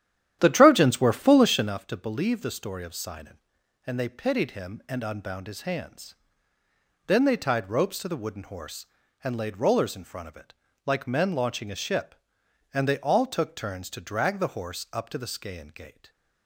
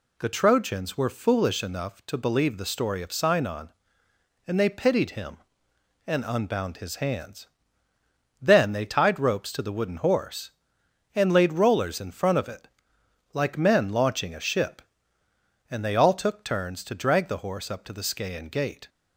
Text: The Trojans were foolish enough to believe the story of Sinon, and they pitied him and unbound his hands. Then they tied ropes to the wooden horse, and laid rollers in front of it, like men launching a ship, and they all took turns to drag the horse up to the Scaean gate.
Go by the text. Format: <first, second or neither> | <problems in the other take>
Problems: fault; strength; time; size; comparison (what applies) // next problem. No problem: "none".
second | starts louder than the rest; strong; until 1.8 s; 11 dB